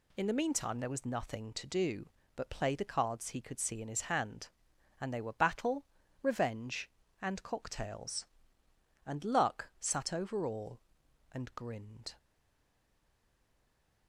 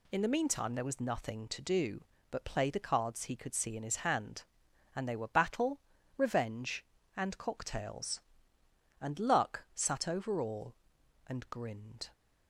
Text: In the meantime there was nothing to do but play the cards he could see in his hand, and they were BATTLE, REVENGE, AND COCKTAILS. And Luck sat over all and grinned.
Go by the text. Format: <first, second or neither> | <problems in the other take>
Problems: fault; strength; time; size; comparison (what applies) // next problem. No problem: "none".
second | stays silent after the last word; noticeable; from 12.1 s on; 1.9 s long